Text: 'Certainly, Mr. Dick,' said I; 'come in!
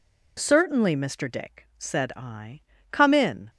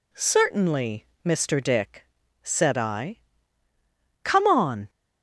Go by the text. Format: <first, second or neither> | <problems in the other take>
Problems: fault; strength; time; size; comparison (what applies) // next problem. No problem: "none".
first | says "on" for "in"; at 4.4 s